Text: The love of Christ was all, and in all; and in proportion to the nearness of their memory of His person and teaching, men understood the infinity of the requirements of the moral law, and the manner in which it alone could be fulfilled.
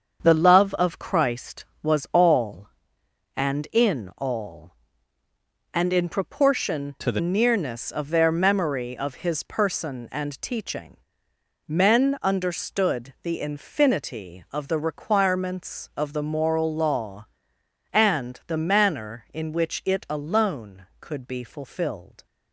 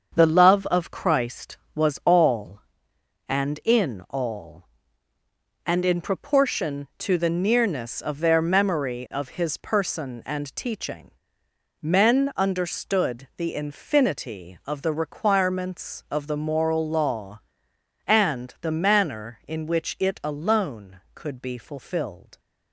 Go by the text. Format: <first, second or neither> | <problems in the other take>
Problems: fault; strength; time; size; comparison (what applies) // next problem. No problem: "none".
second | starts louder than the rest; until 1.2 s; 7 dB; also in the second // changes voice from "to" to "the"; from 7.0 to 7.1 s; 0.1 s long